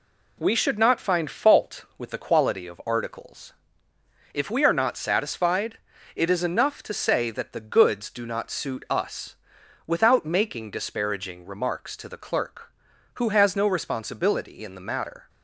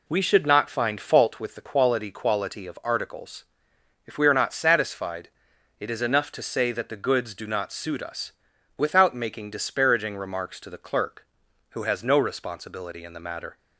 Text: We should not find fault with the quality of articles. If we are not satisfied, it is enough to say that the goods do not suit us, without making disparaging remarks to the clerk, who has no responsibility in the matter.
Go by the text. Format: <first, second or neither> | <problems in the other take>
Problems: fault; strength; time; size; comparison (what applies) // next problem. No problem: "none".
first | says "quality" twice; at 2.1 s